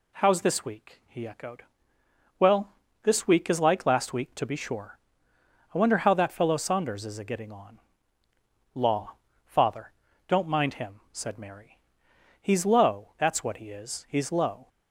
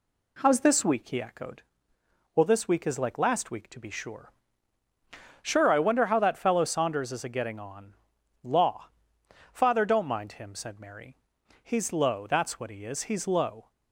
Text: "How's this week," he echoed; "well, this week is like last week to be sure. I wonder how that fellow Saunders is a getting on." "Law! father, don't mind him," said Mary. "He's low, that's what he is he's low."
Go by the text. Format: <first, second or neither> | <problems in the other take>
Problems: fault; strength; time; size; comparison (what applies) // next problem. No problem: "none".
first | says "sure" twice; at 5.4 s